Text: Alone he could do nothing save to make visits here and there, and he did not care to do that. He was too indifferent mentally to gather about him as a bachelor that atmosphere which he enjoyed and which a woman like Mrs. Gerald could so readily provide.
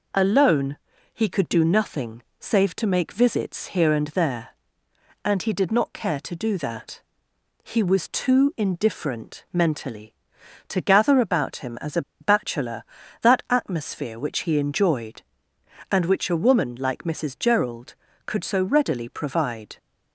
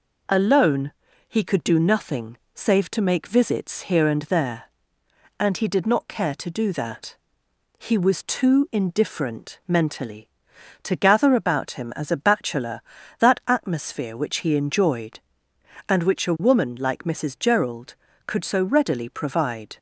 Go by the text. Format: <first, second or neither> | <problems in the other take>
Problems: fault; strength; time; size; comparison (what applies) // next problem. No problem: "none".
second | pauses between "Alone" and "he"; at 0.7 s; 0.38 s long; also in the second // pauses between "nothing" and "save"; slight; at 2.2 s; 0.18 s long; slight in the second // pauses between "a" and "bachelor"; slight; at 12.0 s; 0.19 s long